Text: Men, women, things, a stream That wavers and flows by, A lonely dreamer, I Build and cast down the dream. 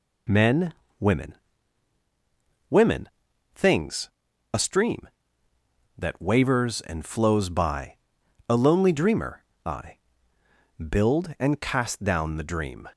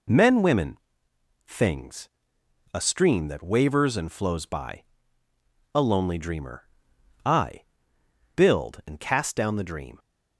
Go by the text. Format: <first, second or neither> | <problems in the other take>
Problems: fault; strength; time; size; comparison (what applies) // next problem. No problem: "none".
second | says "women" twice; at 2.6 s // pauses between "I" and "Build"; noticeable; at 9.9 s; 0.94 s long; noticeable in the second